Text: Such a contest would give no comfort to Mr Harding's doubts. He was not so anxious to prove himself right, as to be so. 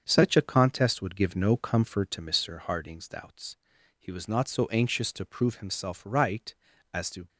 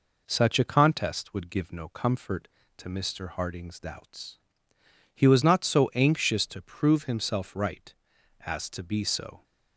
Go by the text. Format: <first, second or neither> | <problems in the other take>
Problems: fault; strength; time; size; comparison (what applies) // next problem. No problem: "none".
second | starts louder than the rest; strong; until 1.0 s; 7.5 dB // stops before "be so"; at 7.2 s